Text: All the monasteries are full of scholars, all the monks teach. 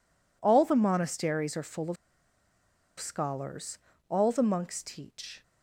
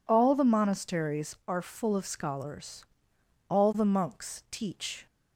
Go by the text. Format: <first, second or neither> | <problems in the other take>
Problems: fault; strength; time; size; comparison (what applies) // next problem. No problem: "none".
second | pauses between "of" and "scholars"; at 1.9 s; 1.0 s long